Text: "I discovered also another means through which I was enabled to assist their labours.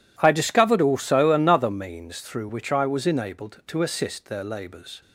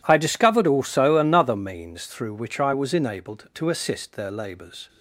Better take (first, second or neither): neither